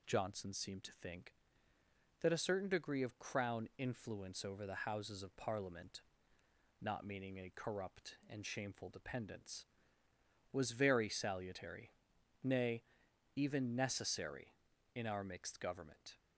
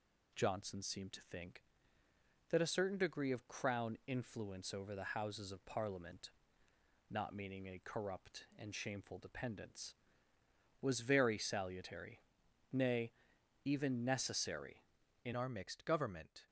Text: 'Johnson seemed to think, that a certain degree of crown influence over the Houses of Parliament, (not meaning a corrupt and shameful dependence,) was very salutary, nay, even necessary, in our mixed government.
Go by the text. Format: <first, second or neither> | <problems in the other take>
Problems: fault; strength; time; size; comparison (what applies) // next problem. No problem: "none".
first | changes voice at "our"; from 15.3 s on; 1.1 s long